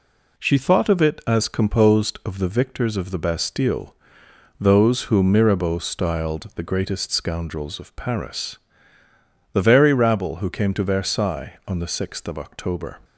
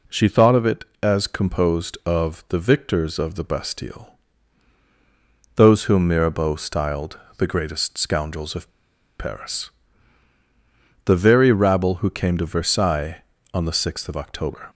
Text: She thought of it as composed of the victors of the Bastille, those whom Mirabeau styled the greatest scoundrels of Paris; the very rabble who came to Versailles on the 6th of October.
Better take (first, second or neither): first